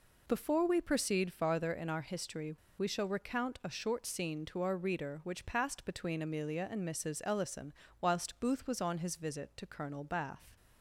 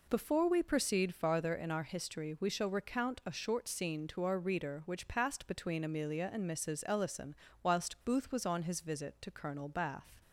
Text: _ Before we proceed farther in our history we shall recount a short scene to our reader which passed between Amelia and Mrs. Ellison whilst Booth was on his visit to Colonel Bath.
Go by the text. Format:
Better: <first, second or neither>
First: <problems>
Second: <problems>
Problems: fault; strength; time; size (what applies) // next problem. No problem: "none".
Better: second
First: pauses between "history" and "we"; slight; at 2.5 s; 0.26 s long // pauses between "Ellison" and "whilst"; slight; at 7.7 s; 0.26 s long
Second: pauses between "Ellison" and "whilst"; slight; at 7.3 s; 0.26 s long